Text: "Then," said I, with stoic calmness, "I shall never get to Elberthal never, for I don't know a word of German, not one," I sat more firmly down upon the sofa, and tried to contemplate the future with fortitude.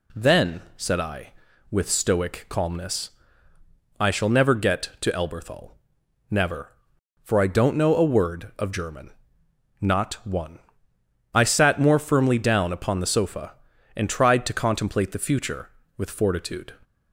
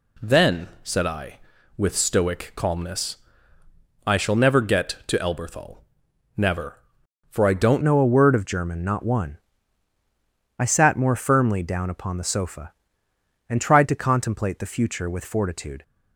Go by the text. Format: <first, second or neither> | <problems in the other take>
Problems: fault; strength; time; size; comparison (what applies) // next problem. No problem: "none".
first | pauses between "Elberthal" and "never"; noticeable; at 5.7 s; 0.58 s long; noticeable in the first // changes voice at "know"; from 7.8 s on; 8.0 s long